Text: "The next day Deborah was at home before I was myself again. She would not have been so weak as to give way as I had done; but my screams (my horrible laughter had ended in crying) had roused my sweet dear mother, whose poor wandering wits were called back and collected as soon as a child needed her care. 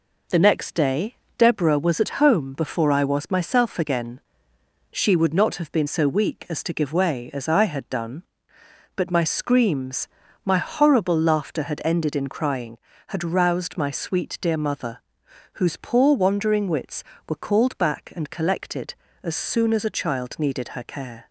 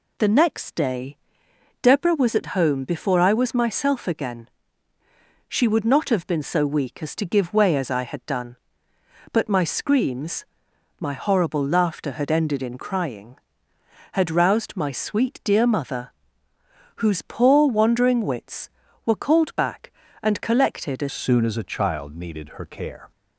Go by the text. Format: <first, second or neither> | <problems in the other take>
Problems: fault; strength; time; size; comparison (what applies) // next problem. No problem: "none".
first | pauses between "day" and "Deborah"; noticeable; at 1.1 s; 0.64 s long; slight in the first // changes voice at "soon"; from 21.0 s on; 2.1 s long